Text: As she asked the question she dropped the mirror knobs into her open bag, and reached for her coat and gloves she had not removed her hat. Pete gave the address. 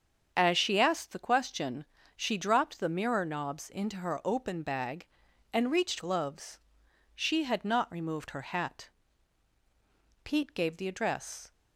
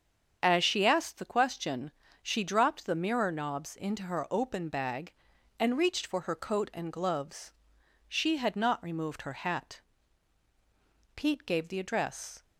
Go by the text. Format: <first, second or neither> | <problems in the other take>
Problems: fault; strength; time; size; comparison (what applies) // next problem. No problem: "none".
second | starts louder than the rest; until 1.3 s; 7 dB; strong in the second // pauses between "question" and "she"; slight; at 1.8 s; 0.32 s long; slight in the second // skips "for her coat and"; at 5.9 s // pauses between "gloves" and "she"; noticeable; at 6.5 s; 0.56 s long; noticeable in the second